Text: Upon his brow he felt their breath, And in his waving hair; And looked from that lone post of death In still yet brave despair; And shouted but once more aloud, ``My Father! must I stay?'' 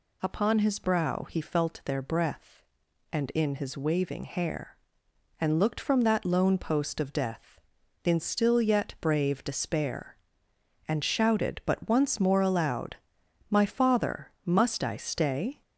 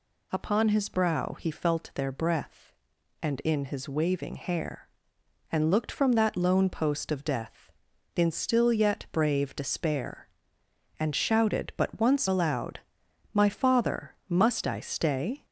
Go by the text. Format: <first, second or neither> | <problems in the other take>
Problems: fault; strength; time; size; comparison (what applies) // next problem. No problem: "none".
first | skips "more"; at 12.2 s